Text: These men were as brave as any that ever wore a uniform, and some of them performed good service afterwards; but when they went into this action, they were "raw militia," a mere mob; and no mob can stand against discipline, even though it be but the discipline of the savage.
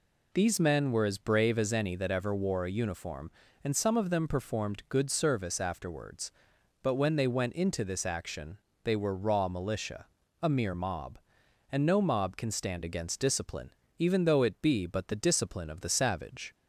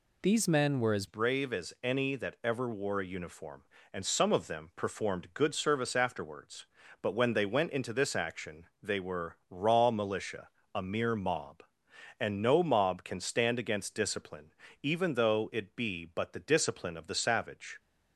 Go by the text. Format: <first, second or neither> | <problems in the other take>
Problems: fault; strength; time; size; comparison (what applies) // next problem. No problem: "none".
first | changes voice at "brave"; from 1.0 s on; 16.7 s long